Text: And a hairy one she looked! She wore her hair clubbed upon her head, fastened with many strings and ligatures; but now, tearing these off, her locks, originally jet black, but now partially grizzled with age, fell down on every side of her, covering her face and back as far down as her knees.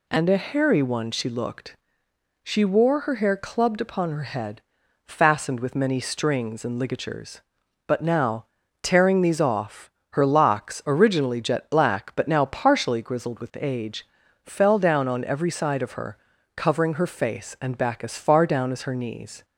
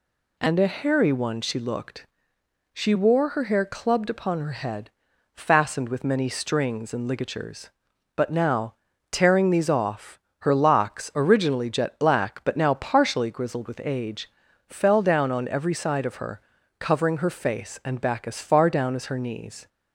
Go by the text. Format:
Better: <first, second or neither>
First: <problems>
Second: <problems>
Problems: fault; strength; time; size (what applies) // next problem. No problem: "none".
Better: neither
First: none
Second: none